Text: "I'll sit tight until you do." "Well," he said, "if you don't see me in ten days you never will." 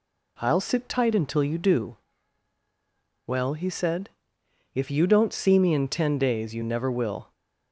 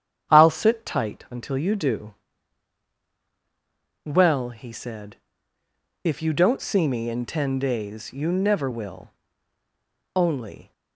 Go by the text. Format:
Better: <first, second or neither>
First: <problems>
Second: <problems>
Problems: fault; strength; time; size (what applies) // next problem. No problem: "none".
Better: first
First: none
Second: starts louder than the rest; strong; until 1.3 s; 9 dB // goes on to say "Only"; from 10.1 s on; 0.56 s long